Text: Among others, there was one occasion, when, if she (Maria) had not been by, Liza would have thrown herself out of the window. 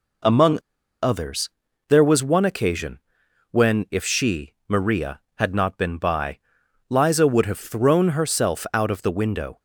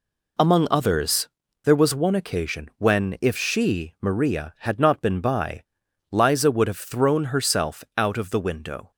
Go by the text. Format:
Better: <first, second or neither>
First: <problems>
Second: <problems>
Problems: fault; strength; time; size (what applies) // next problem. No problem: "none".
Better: second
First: pauses between "Among" and "others"; at 0.5 s; 0.45 s long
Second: none